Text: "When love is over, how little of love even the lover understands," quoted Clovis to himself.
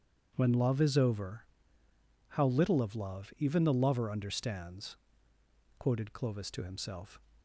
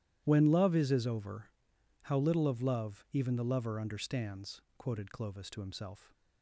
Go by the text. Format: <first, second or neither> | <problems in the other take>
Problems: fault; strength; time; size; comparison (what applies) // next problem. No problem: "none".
first | starts louder than the rest; strong; until 1.2 s; 12 dB; strong in the first // says "is" twice; at 0.9 s